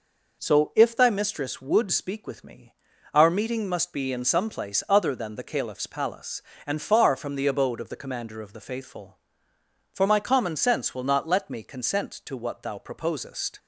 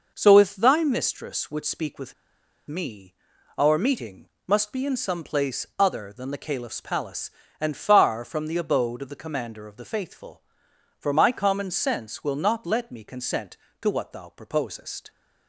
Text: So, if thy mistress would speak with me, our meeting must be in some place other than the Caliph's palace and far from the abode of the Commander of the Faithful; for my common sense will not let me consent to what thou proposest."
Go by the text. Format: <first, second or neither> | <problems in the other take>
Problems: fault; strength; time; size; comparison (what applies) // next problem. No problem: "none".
first | pauses between "with" and "me"; noticeable; at 2.1 s; 0.54 s long // pauses between "meeting" and "must"; slight; at 4.2 s; 0.18 s long